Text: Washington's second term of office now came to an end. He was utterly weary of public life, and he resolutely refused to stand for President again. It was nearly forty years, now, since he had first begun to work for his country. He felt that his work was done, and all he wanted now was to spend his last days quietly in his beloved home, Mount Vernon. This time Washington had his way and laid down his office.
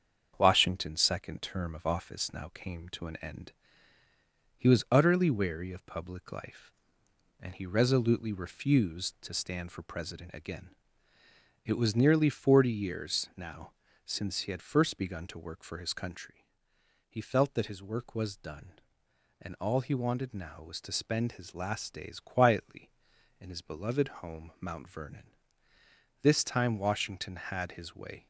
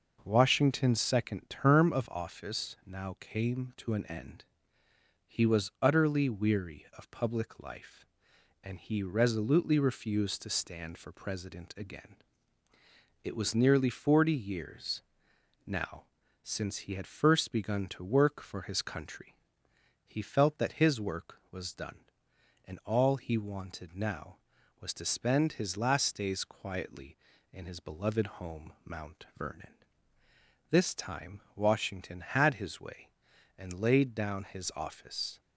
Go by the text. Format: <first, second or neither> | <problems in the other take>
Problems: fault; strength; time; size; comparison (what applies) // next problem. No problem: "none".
second | starts louder than the rest; strong; until 1.3 s; 7 dB // stops before "and laid down his office"; at 28.2 s